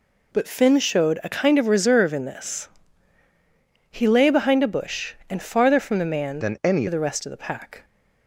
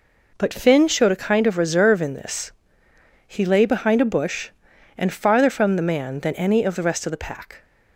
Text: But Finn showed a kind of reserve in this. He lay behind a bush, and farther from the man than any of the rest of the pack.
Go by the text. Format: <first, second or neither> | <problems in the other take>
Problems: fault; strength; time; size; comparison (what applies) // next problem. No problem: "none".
second | changes voice from "than" to "any"; from 6.4 to 6.8 s; 0.4 s long